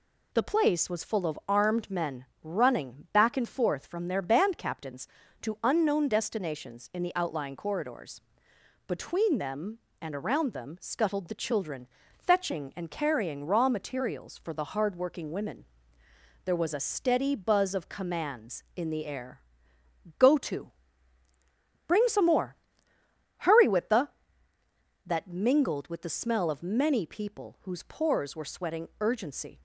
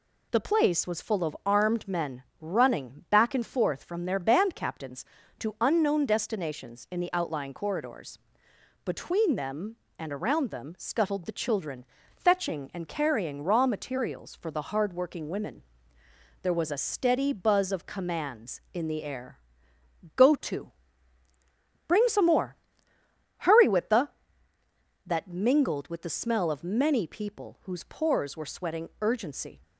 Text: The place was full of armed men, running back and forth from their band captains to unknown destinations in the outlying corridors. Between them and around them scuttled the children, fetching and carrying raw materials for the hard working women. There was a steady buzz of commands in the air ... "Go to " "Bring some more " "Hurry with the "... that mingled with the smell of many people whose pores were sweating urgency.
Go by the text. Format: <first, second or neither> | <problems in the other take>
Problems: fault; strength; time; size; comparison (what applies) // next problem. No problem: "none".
neither | none